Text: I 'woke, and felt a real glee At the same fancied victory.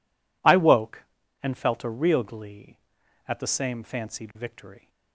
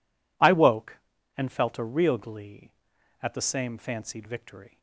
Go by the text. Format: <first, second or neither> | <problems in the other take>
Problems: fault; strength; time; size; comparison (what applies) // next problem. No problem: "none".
neither | none